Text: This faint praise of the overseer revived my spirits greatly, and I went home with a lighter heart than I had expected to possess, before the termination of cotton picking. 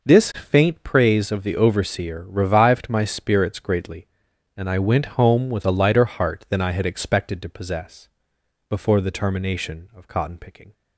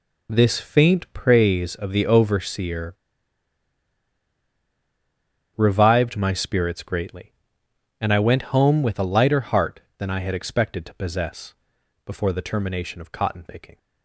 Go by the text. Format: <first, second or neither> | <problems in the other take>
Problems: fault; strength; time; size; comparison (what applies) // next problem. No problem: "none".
first | pauses between "overseer" and "revived"; strong; at 2.9 s; 2.6 s long